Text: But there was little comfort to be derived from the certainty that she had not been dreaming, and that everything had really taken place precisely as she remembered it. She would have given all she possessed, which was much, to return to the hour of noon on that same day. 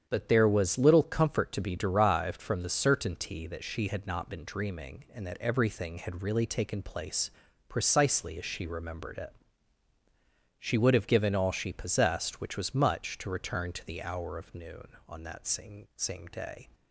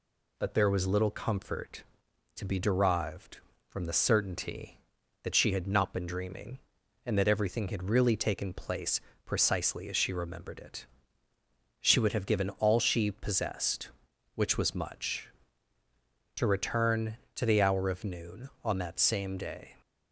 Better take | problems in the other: second | starts louder than the rest; strong; until 1.0 s; 8 dB // pauses between "place" and "precisely"; at 7.3 s; 0.38 s long; slight in the second // says "same" twice; at 15.9 s

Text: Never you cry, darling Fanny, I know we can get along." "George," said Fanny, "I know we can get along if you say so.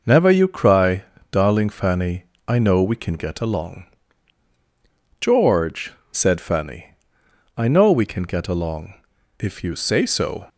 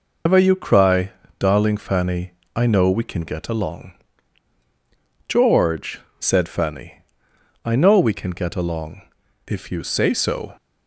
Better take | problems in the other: first | loses the start of "Never"; at 0.2 s; 135 ms // pauses between "along" and "if"; at 9.0 s; 0.44 s long; also in the first

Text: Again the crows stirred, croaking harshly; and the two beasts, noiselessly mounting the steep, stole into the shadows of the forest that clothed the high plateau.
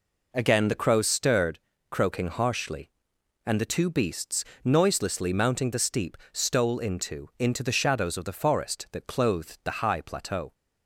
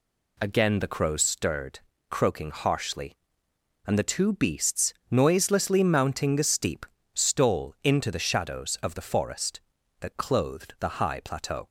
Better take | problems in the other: second | says "into" twice; at 7.3 s

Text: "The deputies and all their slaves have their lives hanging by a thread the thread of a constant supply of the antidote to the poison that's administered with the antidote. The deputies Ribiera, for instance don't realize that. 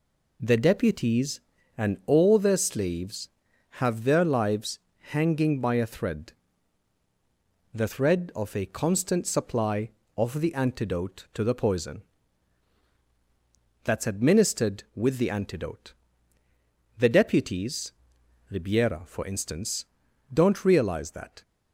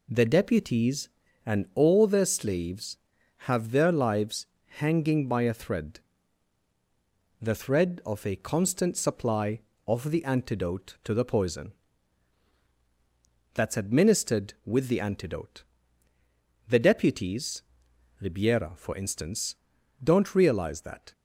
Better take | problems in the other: neither | pauses between "lives" and "hanging"; slight; the same in both // pauses between "thread" and "the"; strong; the same in both // pauses between "poison" and "that's"; strong; the same in both // pauses between "deputies" and "Ribiera"; noticeable; the same in both // pauses between "instance" and "don't"; noticeable; the same in both

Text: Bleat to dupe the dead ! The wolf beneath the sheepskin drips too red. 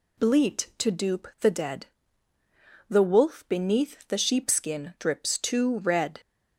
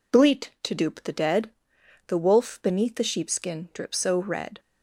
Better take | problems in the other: first | says "so" for "too"; at 3.9 s

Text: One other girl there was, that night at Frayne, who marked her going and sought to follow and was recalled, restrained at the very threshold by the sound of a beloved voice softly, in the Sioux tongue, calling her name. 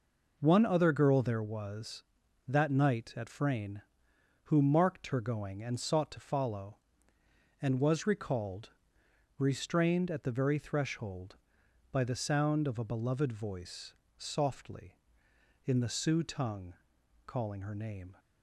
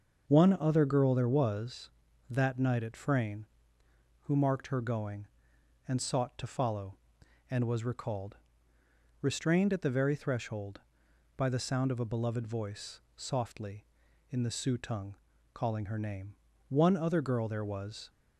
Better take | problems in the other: first | starts louder than the rest; until 1.3 s; 6.5 dB // pauses between "voice" and "softly"; slight; at 12.9 s; 0.18 s long; slight in the first // goes on to say "One other girl there was"; from 16.6 s on; 1.4 s long

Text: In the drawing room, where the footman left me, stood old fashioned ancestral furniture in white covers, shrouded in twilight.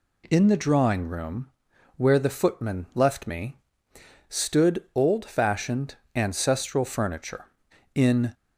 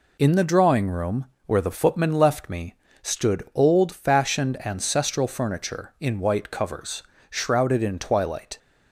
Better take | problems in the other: second | pauses between "fashioned" and "ancestral"; slight; at 5.9 s; 0.20 s long // stops before "white covers shrouded in twilight"; at 8.3 s

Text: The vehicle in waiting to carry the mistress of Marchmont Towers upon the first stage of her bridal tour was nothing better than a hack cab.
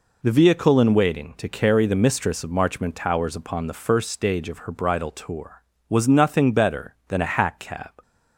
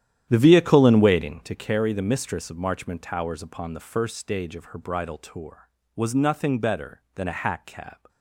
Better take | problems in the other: first | starts louder than the rest; strong; until 1.7 s; 11 dB

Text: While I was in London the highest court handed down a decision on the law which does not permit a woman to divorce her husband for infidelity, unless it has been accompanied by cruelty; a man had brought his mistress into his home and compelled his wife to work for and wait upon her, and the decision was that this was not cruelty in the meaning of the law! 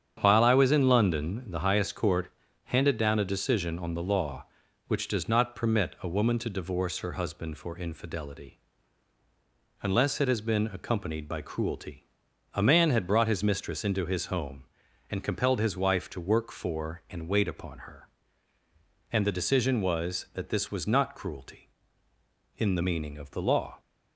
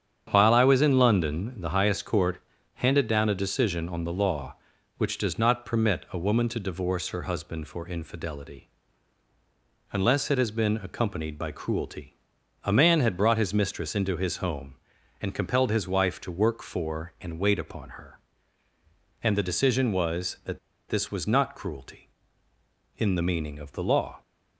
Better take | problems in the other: first | starts louder than the rest; strong; until 1.3 s; 8.5 dB; strong in the first // pauses between "court" and "handed"; slight; at 2.3 s; 0.36 s long; slight in the first // pauses between "that" and "this"; slight; at 20.5 s; 0.30 s long

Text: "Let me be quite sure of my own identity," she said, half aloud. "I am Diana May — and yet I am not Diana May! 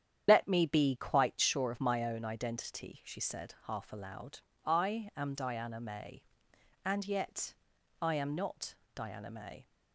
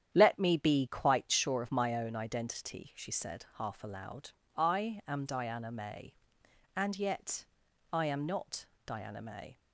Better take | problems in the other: second | loses the start of "Let"; at 0.2 s; 60 ms // starts louder than the rest; strong; until 1.2 s; 9 dB; strong in the second // pauses between "yet" and "I"; noticeable; at 7.5 s; 0.48 s long; noticeable in the second // pauses between "not" and "Diana"; slight; at 8.7 s; 0.22 s long; slight in the second

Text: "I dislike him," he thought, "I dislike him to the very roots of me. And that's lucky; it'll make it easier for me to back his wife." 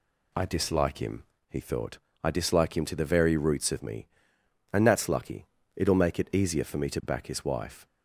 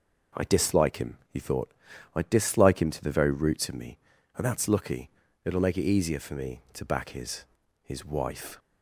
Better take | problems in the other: first | says "his" twice; at 7.8 s

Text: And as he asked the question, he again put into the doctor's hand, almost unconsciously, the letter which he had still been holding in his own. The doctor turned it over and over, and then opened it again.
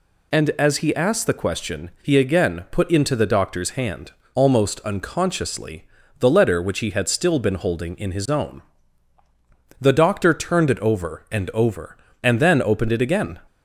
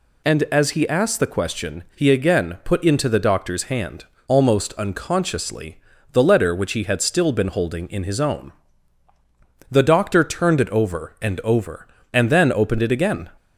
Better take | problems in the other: neither | none

